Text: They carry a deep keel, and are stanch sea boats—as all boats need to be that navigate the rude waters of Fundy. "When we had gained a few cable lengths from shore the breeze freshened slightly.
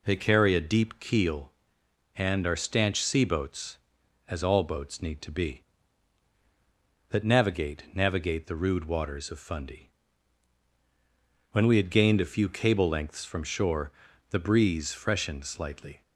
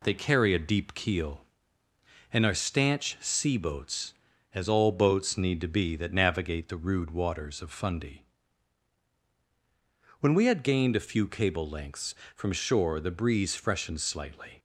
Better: second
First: says "navigate" twice; at 7.9 s // pauses between "shore" and "the"; at 13.9 s; 0.40 s long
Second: none

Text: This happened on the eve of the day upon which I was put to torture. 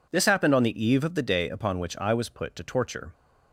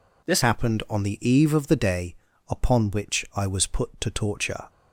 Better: first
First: none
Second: changes voice at "happened"; from 0.4 s on; 4.2 s long // pauses between "day" and "upon"; slight; at 2.1 s; 0.34 s long

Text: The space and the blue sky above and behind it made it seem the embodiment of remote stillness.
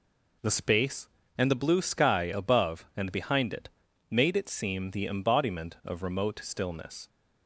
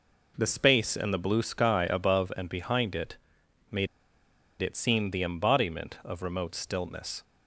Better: first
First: pauses between "it" and "made"; at 3.6 s; 0.40 s long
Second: pauses between "it" and "made"; noticeable; at 3.1 s; 0.56 s long // pauses between "made" and "it"; noticeable; at 3.8 s; 0.74 s long

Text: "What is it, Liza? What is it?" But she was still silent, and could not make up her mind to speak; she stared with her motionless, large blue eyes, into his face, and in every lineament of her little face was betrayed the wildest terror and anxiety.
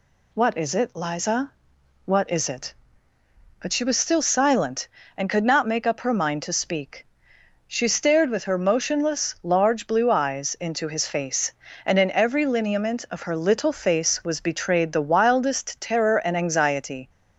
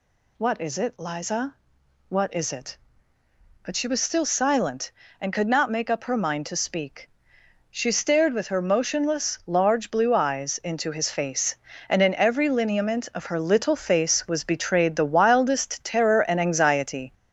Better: first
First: none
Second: gets louder; noticeable; throughout; 5.5 dB

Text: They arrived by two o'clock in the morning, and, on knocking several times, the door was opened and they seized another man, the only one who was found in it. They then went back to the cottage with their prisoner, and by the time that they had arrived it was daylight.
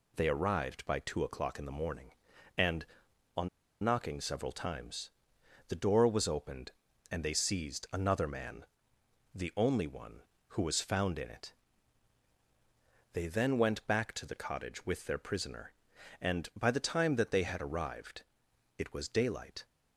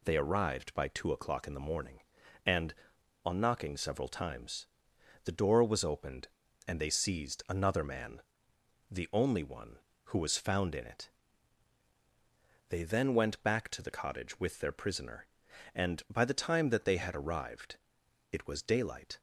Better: second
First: pauses between "on" and "knocking"; slight; at 3.4 s; 0.34 s long // pauses between "arrived" and "it"; noticeable; at 18.2 s; 0.54 s long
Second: pauses between "arrived" and "it"; noticeable; at 17.7 s; 0.54 s long

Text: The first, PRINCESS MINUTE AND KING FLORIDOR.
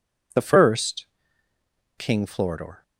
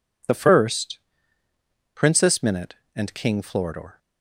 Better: second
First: skips "PRINCESS MINUTE AND"; at 1.5 s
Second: none

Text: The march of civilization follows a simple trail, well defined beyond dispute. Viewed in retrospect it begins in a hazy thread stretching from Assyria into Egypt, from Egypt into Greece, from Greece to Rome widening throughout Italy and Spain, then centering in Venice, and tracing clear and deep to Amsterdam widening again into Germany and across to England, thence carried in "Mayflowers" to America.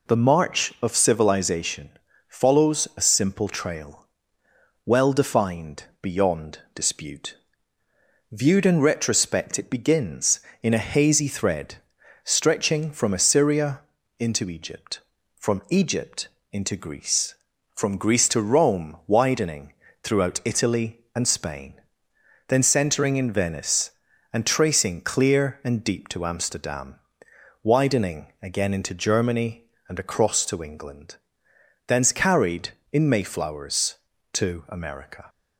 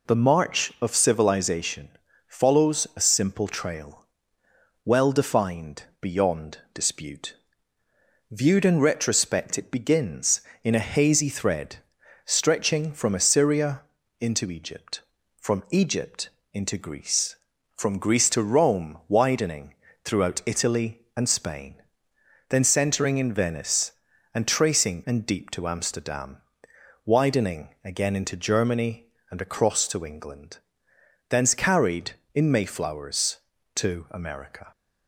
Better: first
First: pauses between "civilization" and "follows"; at 1.8 s; 0.38 s long // pauses between "beyond" and "dispute"; slight; at 6.5 s; 0.16 s long // pauses between "thread" and "stretching"; noticeable; at 11.7 s; 0.46 s long // pauses between "Assyria" and "into"; at 13.7 s; 0.40 s long // pauses between "Egypt" and "into"; slight; at 16.2 s; 0.24 s long // pauses between "widening" and "throughout"; slight; at 19.7 s; 0.30 s long // pauses between "Amsterdam" and "widening"; noticeable; at 26.9 s; 0.66 s long // pauses between "widening" and "again"; slight; at 28.2 s; 0.16 s long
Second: pauses between "civilization" and "follows"; at 1.8 s; 0.38 s long // pauses between "beyond" and "dispute"; slight; at 6.5 s; 0.16 s long // pauses between "thread" and "stretching"; noticeable; at 11.7 s; 0.46 s long // pauses between "Assyria" and "into"; at 13.8 s; 0.40 s long // pauses between "Egypt" and "into"; slight; at 16.2 s; 0.24 s long // pauses between "widening" and "throughout"; slight; at 19.7 s; 0.30 s long // skips "clear"; at 25.0 s // pauses between "Amsterdam" and "widening"; noticeable; at 26.3 s; 0.66 s long // pauses between "widening" and "again"; slight; at 27.6 s; 0.16 s long

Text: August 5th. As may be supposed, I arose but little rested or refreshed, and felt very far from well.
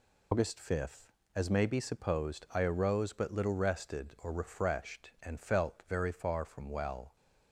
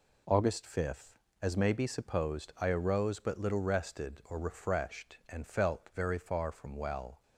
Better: second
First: loses the start of "August"; at 0.3 s; 110 ms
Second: none

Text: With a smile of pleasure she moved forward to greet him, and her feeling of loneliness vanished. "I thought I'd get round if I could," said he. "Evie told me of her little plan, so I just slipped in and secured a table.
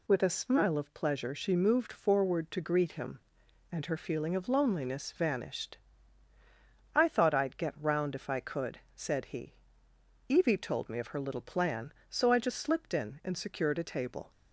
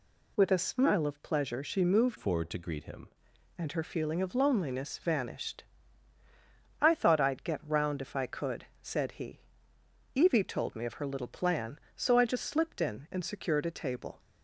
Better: first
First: none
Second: changes voice from "forward" to "him"; from 2.1 to 3.0 s; 0.9 s long

